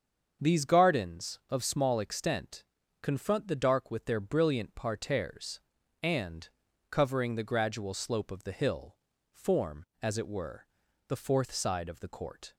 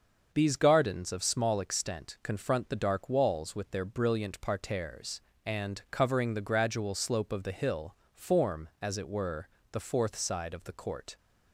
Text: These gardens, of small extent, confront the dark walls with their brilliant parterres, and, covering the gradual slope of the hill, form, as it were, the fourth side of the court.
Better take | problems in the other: second | starts louder than the rest; until 1.5 s; 7 dB; also in the second // skips "walls"; at 3.8 s

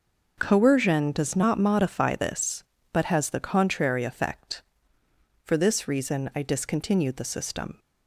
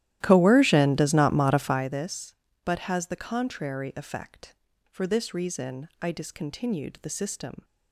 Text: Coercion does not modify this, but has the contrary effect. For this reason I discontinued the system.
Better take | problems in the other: first | starts louder than the rest; strong; until 2.0 s; 13.5 dB

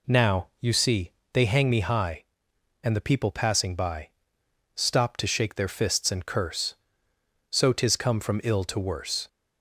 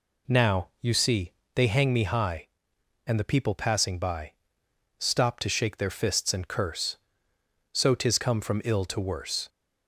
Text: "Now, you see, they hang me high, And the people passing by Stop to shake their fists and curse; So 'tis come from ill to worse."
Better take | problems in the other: neither | pauses between "by" and "Stop"; noticeable; the same in both

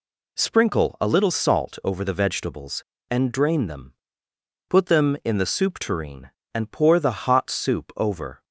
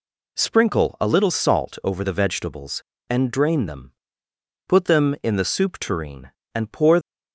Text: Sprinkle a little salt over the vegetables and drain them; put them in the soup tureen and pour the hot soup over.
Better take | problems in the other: first | stops before "the hot soup over"; at 7.0 s

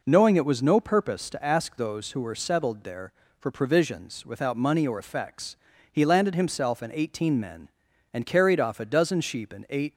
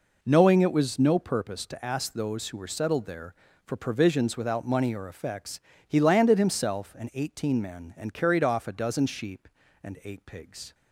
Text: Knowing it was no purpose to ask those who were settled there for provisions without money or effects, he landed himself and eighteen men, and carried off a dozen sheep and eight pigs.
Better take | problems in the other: second | stops before "pigs"; at 9.9 s

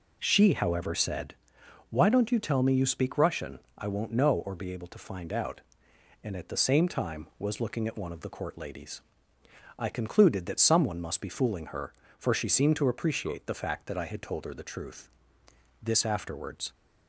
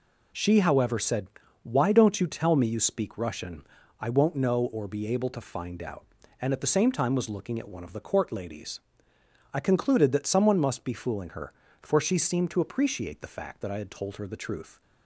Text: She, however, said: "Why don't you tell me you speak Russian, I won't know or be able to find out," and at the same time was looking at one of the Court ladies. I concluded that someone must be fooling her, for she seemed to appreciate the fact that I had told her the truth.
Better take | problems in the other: second | goes on to say "This afterwards"; noticeable; from 15.8 s on; 0.92 s long

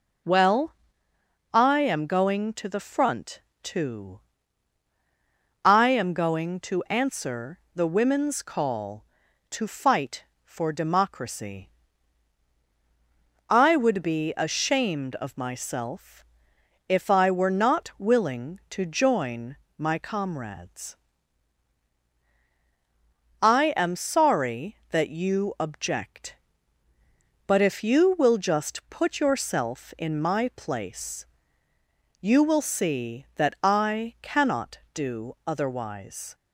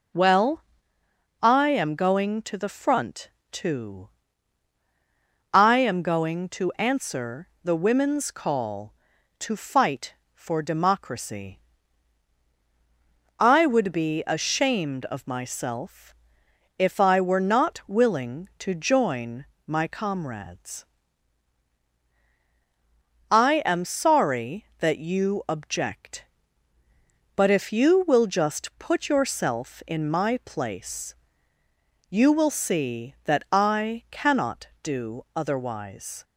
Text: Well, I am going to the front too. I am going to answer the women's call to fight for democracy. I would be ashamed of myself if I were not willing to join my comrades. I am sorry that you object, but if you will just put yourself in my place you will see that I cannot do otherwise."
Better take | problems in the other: neither | pauses between "front" and "too"; slight; the same in both // pauses between "myself" and "if"; noticeable; the same in both // pauses between "join" and "my"; slight; the same in both // pauses between "place" and "you"; noticeable; the same in both

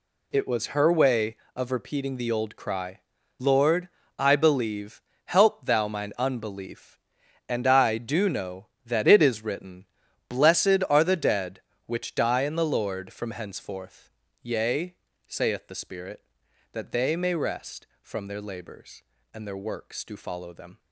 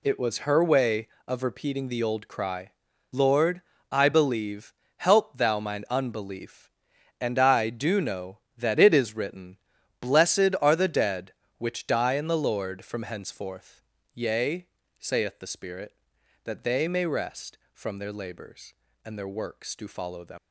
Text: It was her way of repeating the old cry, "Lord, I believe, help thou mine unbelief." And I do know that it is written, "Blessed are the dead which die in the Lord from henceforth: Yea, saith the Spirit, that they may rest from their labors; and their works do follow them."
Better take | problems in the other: first | leaves "them" unfinished; at 20.3 s; 120 ms

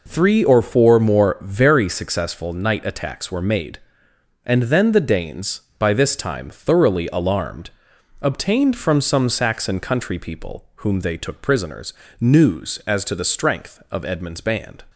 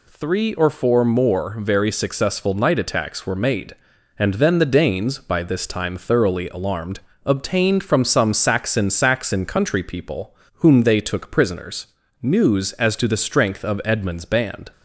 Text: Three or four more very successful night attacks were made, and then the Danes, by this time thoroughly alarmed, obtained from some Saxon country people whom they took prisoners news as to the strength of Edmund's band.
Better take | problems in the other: first | says "Saxon" twice; at 8.8 s // pauses between "people" and "whom"; slight; at 10.3 s; 0.22 s long // pauses between "prisoners" and "news"; slight; at 11.8 s; 0.32 s long; slight in the first

